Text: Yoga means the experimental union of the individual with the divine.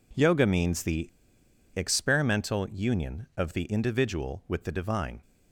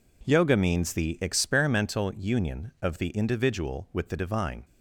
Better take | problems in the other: second | pauses between "the" and "experimental"; noticeable; at 1.0 s; 0.65 s long

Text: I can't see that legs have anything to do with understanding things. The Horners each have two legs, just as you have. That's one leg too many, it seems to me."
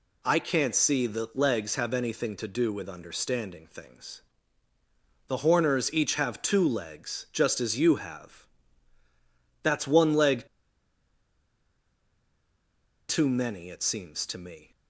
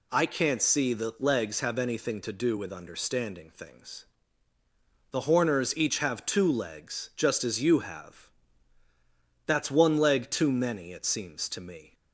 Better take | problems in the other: second | pauses between "leg" and "too"; strong; at 10.4 s; 2.6 s long

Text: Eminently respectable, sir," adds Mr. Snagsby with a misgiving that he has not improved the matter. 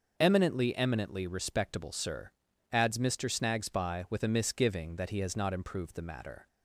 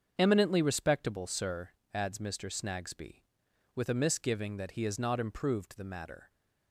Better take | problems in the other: second | starts louder than the rest; noticeable; until 1.2 s; 6 dB; also in the second // says "Eminently" twice; at 0.7 s

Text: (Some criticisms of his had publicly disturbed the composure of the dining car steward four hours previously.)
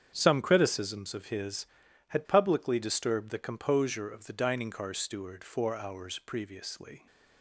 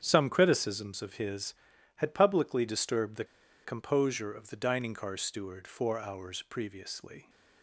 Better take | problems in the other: first | starts louder than the rest; strong; until 1.0 s; 8 dB; strong in the first // pauses between "the" and "composure"; at 3.2 s; 0.40 s long

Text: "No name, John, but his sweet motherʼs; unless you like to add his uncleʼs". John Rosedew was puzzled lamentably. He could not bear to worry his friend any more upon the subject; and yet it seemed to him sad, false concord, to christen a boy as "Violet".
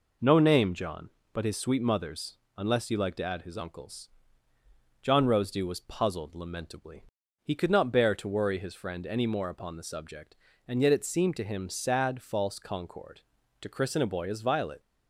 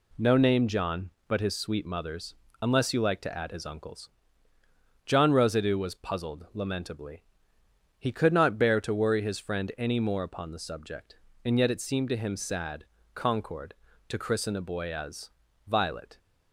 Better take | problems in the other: first | skips "false"; at 12.9 s // pauses between "as" and "Violet"; slight; at 15.3 s; 0.36 s long

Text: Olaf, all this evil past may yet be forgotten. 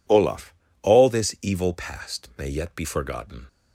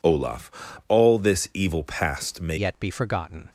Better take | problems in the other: first | changes voice at "yet"; from 2.5 s on; 0.9 s long

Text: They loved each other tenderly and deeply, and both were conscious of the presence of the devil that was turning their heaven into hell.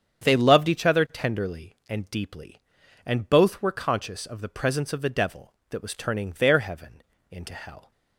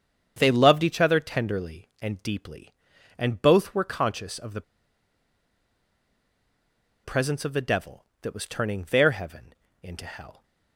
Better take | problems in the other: first | starts louder than the rest; strong; until 1.3 s; 7.5 dB; strong in the first // pauses between "the" and "presence"; strong; at 4.6 s; 2.4 s long // pauses between "heaven" and "into"; slight; at 9.5 s; 0.28 s long; slight in the first

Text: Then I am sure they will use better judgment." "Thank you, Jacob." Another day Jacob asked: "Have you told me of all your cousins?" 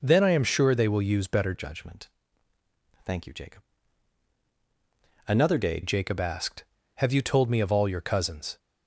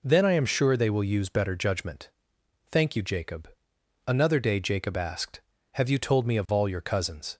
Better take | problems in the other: second | changes voice from "judgment" to "day"; from 1.5 to 5.8 s; 4.3 s long

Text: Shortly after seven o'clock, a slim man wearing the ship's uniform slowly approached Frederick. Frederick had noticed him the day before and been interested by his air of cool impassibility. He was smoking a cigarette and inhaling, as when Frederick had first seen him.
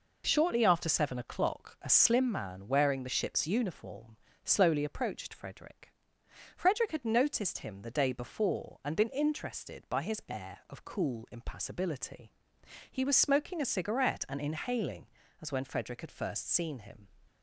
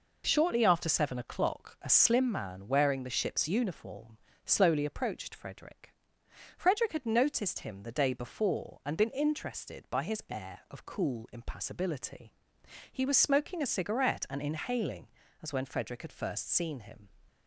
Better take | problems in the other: neither | pauses between "uniform" and "slowly"; slight; the same in both

